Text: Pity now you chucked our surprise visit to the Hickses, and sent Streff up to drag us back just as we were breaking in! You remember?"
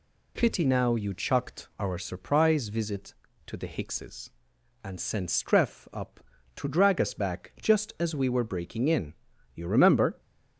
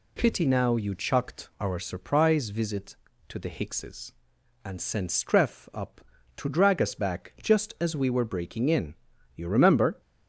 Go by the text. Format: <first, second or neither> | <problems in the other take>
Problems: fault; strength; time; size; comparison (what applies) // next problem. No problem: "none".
neither | none